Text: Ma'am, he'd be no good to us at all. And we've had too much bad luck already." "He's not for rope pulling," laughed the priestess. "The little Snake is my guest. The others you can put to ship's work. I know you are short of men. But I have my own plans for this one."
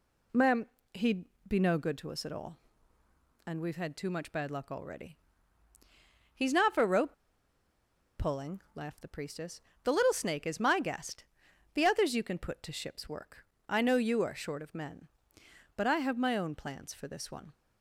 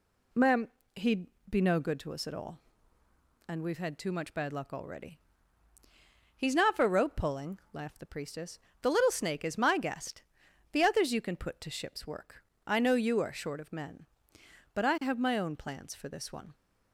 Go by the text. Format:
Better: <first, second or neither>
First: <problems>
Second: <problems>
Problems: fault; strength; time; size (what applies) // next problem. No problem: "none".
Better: second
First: pauses between "he'd" and "be"; slight; at 1.2 s; 0.24 s long // pauses between "rope" and "pulling"; at 7.1 s; 1.0 s long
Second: pauses between "he'd" and "be"; slight; at 1.2 s; 0.24 s long